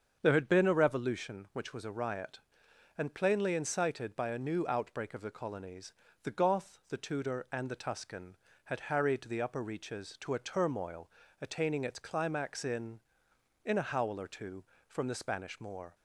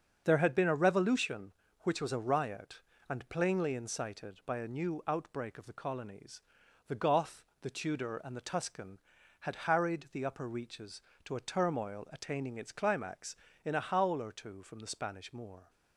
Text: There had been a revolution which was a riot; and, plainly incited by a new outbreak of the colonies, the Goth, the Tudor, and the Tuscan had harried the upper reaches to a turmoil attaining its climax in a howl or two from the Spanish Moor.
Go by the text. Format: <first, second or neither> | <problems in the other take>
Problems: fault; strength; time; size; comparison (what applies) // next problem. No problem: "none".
second | starts louder than the rest; until 1.2 s; 7 dB; also in the second // pauses between "turmoil" and "attaining"; slight; at 11.0 s; 0.32 s long // says "in" twice; at 13.6 s